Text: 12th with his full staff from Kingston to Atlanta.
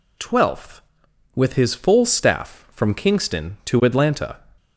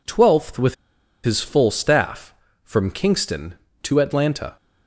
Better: first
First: none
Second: pauses between "with" and "his"; noticeable; at 0.7 s; 0.49 s long

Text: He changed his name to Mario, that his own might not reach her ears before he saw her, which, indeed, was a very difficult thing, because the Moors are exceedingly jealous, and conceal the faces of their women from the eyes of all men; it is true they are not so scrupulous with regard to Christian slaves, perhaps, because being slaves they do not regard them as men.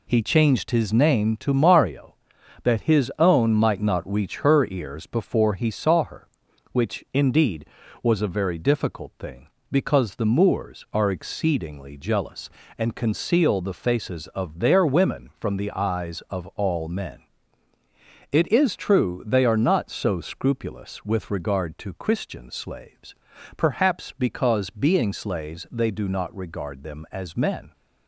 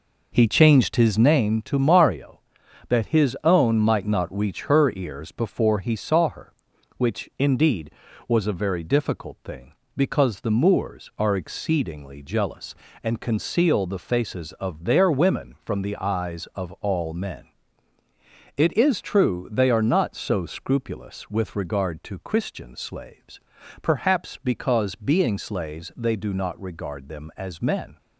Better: first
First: none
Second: starts louder than the rest; noticeable; until 1.4 s; 4.5 dB

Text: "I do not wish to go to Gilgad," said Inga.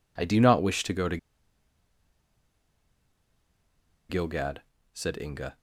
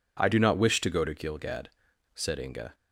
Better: second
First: pauses between "to" and "Gilgad"; strong; at 1.1 s; 2.9 s long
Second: none

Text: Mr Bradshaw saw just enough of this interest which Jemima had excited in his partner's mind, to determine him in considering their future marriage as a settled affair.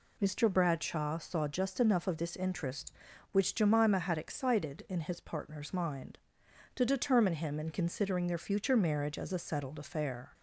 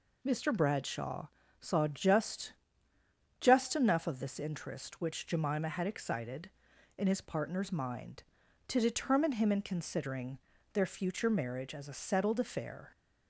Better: first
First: none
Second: pauses between "Bradshaw" and "saw"; slight; at 1.2 s; 0.34 s long // says "just" twice; at 3.3 s // pauses between "considering" and "their"; slight; at 10.3 s; 0.36 s long

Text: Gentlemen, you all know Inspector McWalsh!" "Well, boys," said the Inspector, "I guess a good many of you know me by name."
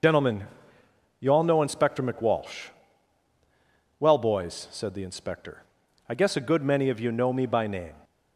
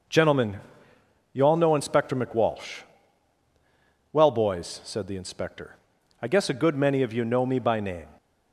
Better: second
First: loses the start of "Gentlemen"; at 0.0 s; 75 ms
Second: none

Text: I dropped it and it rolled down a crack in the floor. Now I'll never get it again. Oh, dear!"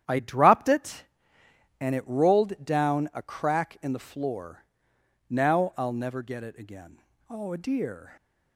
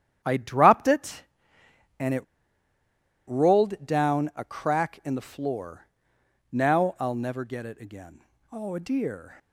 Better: first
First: starts louder than the rest; strong; until 1.8 s; 10 dB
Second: starts louder than the rest; strong; until 1.2 s; 10 dB // pauses between "it" and "rolled"; at 2.2 s; 1.0 s long

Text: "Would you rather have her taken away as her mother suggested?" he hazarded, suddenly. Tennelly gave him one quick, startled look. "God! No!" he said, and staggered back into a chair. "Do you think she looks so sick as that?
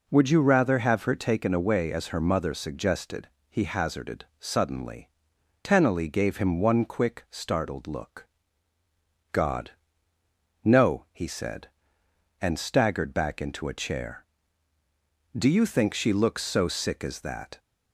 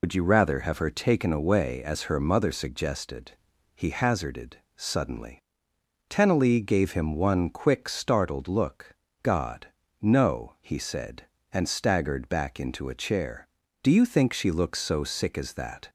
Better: first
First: none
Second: loses the start of "Would"; at 0.0 s; 80 ms

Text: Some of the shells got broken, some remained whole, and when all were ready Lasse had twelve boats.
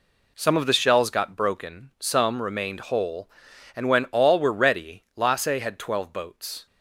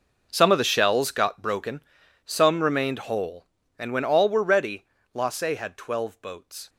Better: first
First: none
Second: gets quieter; strong; throughout; 16.5 dB // pauses between "ready" and "Lasse"; slight; at 4.8 s; 0.30 s long

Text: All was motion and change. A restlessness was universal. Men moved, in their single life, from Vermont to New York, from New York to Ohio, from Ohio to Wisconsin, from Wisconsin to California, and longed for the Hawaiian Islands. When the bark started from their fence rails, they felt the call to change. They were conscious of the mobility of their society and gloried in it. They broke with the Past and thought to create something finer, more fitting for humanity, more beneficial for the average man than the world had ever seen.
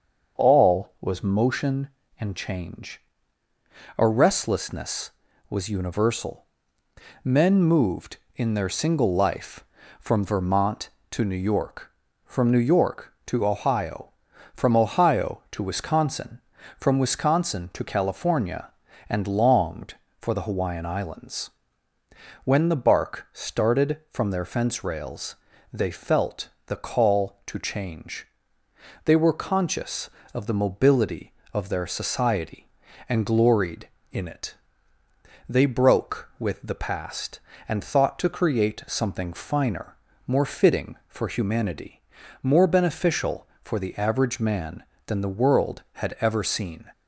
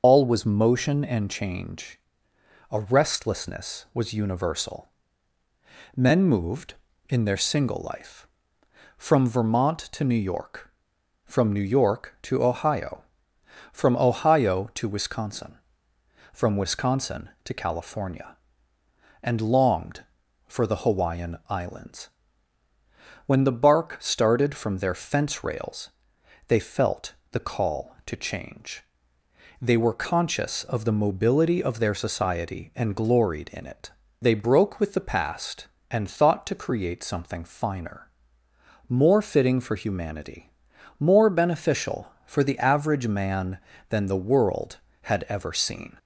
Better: first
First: starts louder than the rest; until 1.4 s; 6.5 dB // pauses between "felt" and "the"; slight; at 26.4 s; 0.18 s long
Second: loses the start of "All"; at 0.0 s; 90 ms // starts louder than the rest; until 1.0 s; 6.5 dB // pauses between "felt" and "the"; slight; at 27.1 s; 0.18 s long

